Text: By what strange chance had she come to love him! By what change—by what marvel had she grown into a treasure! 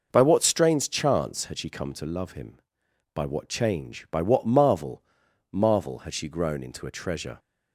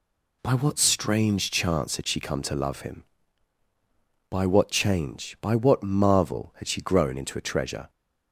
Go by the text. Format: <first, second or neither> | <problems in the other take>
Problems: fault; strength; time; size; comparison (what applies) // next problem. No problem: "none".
second | says "marvel" twice; at 5.5 s